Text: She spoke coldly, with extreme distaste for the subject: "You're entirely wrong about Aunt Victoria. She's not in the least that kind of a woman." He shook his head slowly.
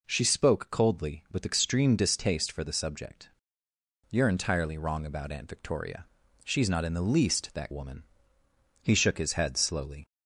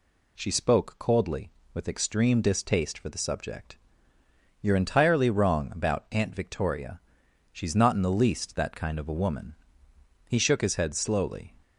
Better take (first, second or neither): second